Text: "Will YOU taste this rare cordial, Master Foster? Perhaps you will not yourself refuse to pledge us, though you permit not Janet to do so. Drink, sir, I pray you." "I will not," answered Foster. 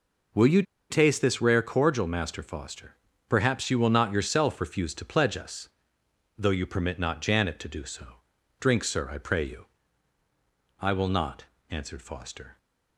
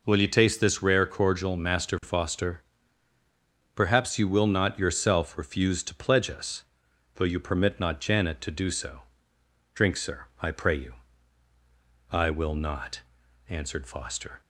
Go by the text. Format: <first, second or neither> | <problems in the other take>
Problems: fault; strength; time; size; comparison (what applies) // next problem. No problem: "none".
second | pauses between "YOU" and "taste"; slight; at 0.6 s; 0.27 s long